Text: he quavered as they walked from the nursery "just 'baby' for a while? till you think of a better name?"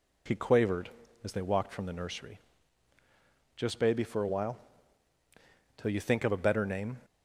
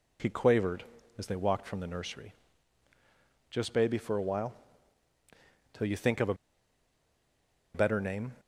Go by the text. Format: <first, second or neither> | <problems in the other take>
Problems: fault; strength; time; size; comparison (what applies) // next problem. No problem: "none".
first | pauses between "nursery" and "just"; at 2.3 s; 1.1 s long; also in the first // pauses between "a" and "better"; strong; at 6.3 s; 1.3 s long